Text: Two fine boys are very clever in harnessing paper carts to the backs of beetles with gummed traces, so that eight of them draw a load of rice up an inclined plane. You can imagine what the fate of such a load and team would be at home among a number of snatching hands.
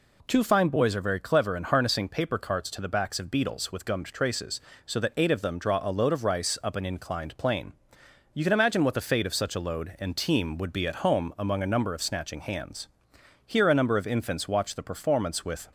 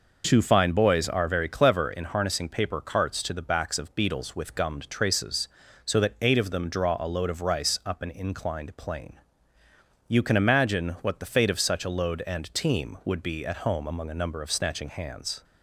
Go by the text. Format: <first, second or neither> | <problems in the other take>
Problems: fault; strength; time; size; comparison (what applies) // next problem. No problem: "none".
second | goes on to say "Here a number of infants watch the performance with"; strong; from 13.4 s on; 2.2 s long